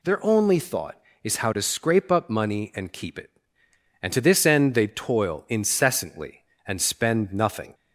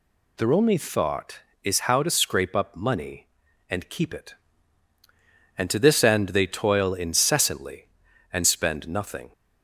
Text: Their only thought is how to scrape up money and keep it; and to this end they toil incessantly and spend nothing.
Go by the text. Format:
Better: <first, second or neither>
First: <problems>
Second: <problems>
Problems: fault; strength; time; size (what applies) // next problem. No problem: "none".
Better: neither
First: none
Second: none